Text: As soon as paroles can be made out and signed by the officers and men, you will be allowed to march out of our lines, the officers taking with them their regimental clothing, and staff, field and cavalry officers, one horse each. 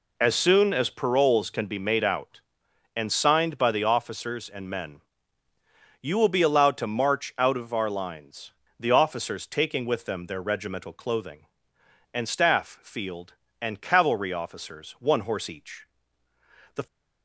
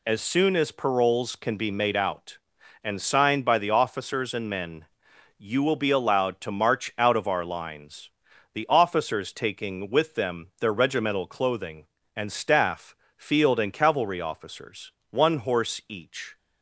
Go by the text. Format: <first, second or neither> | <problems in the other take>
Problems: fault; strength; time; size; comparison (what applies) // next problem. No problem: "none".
second | goes on to say "The"; slight; from 16.7 s on; 0.10 s long